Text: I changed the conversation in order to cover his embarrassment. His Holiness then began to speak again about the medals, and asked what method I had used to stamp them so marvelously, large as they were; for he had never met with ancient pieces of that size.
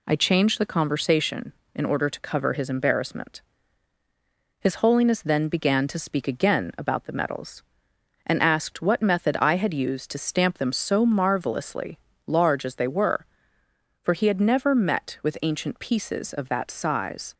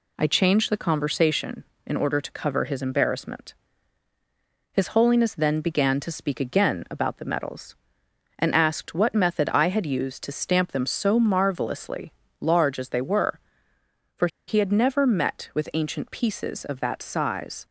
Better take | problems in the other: first | pauses between "for" and "he"; slight; at 14.2 s; 0.20 s long

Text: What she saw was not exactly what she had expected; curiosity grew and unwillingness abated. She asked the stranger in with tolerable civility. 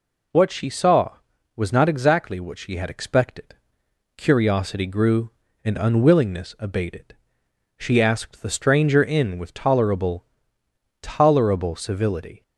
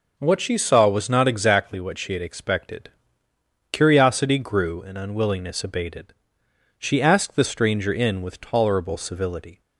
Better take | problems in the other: second | says "tolerable" twice; at 11.0 s

